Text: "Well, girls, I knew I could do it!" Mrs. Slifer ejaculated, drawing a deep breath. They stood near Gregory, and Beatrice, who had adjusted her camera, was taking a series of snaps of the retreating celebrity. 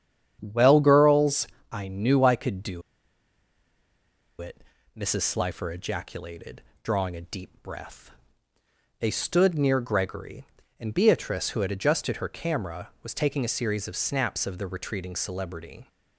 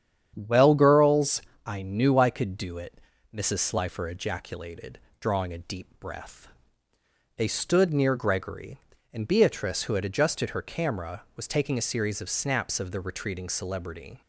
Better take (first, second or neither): second